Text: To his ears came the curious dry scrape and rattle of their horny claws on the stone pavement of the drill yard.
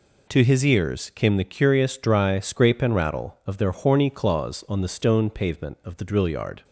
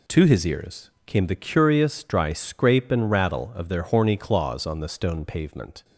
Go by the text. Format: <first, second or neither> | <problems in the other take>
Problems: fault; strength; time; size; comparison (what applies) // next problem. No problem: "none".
first | pauses between "ears" and "came"; slight; at 0.9 s; 0.16 s long // stops before "of the drill yard"; at 5.8 s